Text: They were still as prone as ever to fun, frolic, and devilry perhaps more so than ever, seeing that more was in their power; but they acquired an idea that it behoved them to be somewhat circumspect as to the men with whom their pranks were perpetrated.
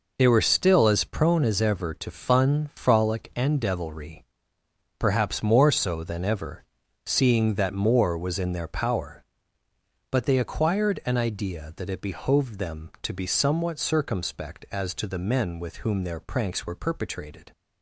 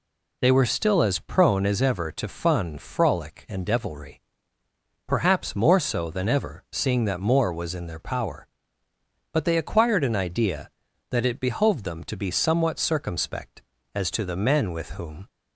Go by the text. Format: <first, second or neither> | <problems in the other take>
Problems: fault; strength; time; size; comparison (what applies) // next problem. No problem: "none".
first | pauses between "devilry" and "perhaps"; noticeable; at 4.2 s; 0.86 s long; noticeable in the first // stops before "their pranks were perpetrated"; at 15.2 s